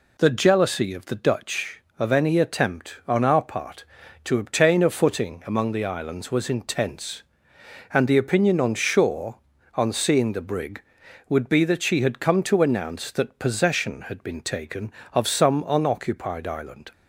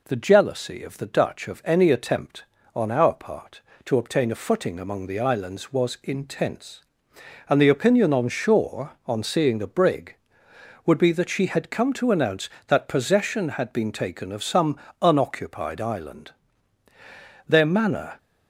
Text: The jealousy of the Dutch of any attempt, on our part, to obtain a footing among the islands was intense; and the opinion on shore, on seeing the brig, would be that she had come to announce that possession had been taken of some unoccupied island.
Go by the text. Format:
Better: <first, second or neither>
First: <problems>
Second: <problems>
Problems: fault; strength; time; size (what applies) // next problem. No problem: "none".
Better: first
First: none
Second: pauses between "some" and "unoccupied"; slight; at 14.7 s; 0.26 s long // goes on to say "Their manner"; noticeable; from 17.4 s on; 0.70 s long